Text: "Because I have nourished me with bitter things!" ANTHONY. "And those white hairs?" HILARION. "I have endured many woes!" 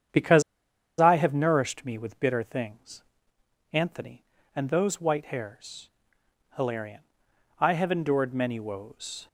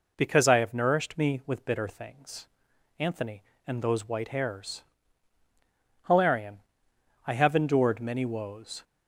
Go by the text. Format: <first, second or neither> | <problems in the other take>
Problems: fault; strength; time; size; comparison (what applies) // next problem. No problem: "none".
second | starts louder than the rest; strong; until 1.7 s; 8.5 dB // pauses between "Because" and "I"; noticeable; at 0.4 s; 0.58 s long